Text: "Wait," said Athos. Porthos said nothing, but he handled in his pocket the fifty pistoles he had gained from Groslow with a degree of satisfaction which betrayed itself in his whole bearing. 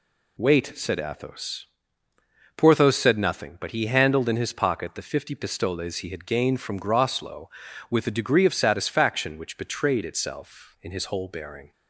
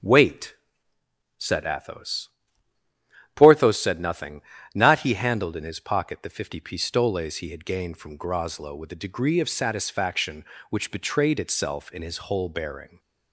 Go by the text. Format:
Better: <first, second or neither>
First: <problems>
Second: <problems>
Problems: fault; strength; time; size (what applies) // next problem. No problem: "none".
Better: first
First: none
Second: starts louder than the rest; until 1.8 s; 7 dB // says "not" for "but"; at 4.7 s